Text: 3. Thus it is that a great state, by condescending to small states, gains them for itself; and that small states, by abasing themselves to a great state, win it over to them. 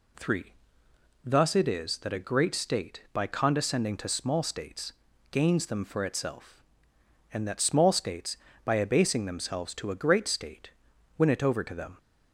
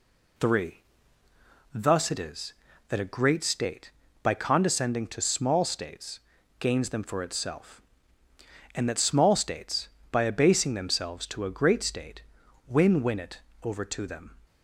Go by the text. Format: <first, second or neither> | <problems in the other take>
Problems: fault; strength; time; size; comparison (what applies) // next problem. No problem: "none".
first | says "win" twice; at 13.0 s // pauses between "it" and "over"; slight; at 13.4 s; 0.22 s long